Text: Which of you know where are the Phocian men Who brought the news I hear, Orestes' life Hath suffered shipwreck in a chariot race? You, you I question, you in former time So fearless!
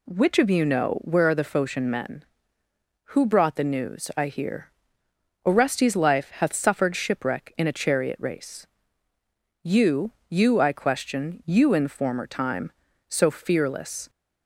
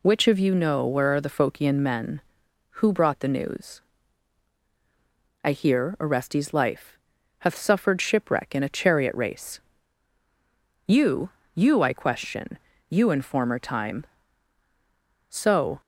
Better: first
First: none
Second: pauses between "news" and "I"; strong; at 3.8 s; 1.6 s long // pauses between "life" and "Hath"; at 6.9 s; 0.44 s long // stops before "fearless"; at 15.8 s

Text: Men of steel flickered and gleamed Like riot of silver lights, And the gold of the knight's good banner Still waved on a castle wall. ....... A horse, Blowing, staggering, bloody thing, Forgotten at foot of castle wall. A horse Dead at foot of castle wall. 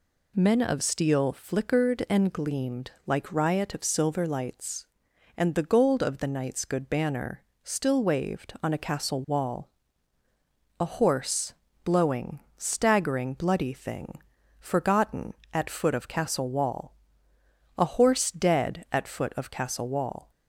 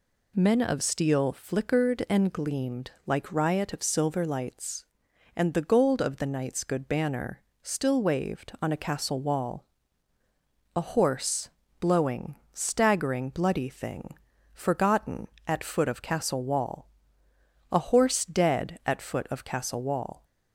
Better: neither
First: pauses between "gleamed" and "Like"; slight; at 2.9 s; 0.16 s long // pauses between "banner" and "Still"; slight; at 7.4 s; 0.20 s long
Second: pauses between "gleamed" and "Like"; slight; at 2.9 s; 0.16 s long // pauses between "banner" and "Still"; slight; at 7.4 s; 0.20 s long

